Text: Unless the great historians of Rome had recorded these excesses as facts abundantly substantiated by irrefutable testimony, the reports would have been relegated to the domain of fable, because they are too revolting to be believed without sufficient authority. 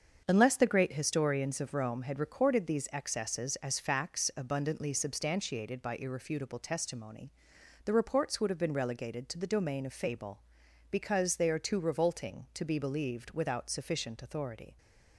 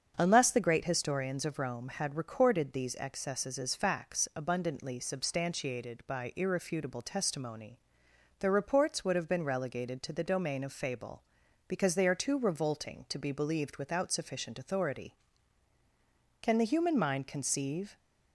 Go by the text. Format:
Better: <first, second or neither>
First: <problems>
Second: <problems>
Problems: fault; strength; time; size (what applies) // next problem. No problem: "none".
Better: first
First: starts louder than the rest; until 1.2 s; 7 dB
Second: starts louder than the rest; strong; until 1.1 s; 7 dB // goes on to say "Can the human mind conceive"; from 16.4 s on; 1.5 s long